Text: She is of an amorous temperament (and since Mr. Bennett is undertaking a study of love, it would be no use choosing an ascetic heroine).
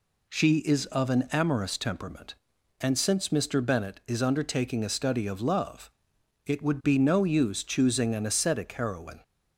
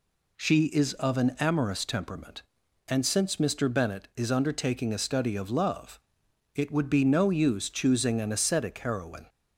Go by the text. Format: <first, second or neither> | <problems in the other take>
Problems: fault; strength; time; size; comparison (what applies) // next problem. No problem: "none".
neither | none